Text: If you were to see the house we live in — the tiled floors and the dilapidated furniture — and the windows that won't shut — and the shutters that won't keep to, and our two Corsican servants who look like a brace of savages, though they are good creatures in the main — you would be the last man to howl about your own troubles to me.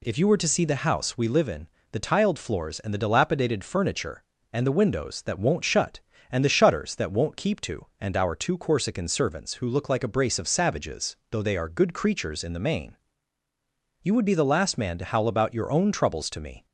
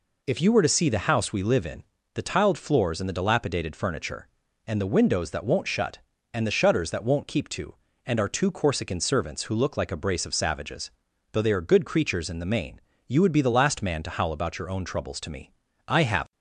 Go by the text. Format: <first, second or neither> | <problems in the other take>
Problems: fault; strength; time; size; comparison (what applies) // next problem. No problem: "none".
first | goes on to say "I have"; slight; from 15.8 s on; 0.44 s long